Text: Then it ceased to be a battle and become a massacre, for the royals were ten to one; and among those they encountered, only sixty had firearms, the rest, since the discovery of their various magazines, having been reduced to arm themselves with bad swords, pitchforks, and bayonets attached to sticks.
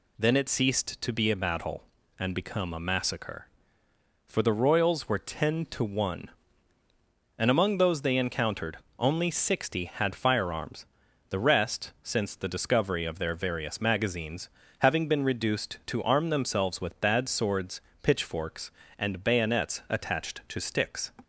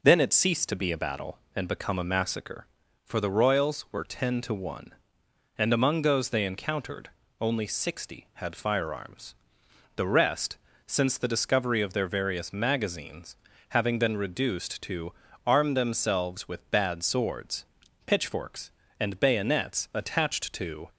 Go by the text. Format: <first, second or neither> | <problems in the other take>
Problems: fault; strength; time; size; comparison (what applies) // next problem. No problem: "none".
first | pauses between "to" and "arm"; slight; at 15.1 s; 0.34 s long // stops before "sticks"; at 20.8 s